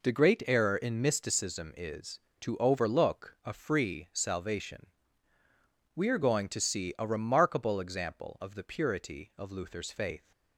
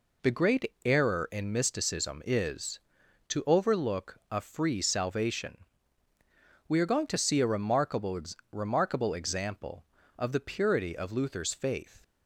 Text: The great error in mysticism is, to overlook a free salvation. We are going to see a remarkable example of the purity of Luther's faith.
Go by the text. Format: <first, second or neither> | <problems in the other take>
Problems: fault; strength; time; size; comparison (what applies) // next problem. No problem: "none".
first | says "remarkable" twice; at 8.5 s